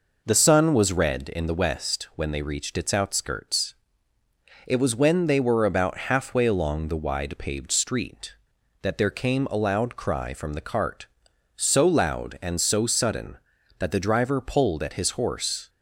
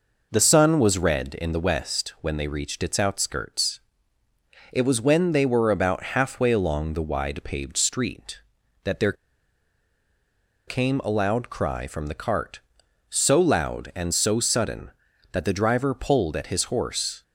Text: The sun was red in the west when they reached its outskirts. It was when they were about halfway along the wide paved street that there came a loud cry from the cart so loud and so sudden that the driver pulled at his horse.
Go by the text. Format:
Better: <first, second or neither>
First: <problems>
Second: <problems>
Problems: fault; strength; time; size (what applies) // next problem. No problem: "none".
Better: first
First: none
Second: pauses between "there" and "came"; strong; at 9.1 s; 1.5 s long